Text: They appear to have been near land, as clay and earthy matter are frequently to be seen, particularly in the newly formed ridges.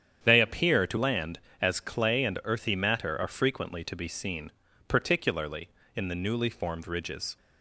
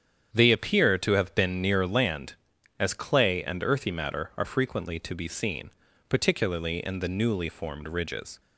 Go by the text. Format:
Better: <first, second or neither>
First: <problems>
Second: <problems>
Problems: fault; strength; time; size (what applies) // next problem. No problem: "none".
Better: second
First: starts louder than the rest; strong; until 1.2 s; 9 dB // skips "have been near"; at 0.9 s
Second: starts louder than the rest; strong; until 1.3 s; 8.5 dB